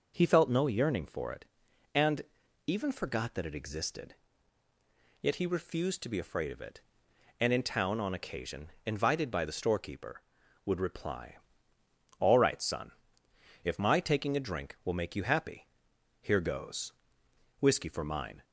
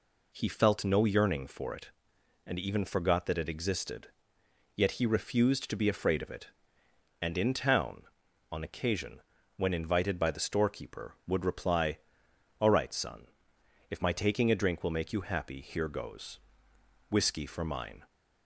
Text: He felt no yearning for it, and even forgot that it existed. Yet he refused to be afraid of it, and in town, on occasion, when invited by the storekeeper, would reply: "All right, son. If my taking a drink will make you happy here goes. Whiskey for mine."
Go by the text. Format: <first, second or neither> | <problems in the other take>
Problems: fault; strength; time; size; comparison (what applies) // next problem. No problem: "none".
second | pauses between "and" and "even"; noticeable; at 2.2 s; 0.48 s long // skips "when"; at 8.7 s // pauses between "happy" and "here"; noticeable; at 15.6 s; 0.56 s long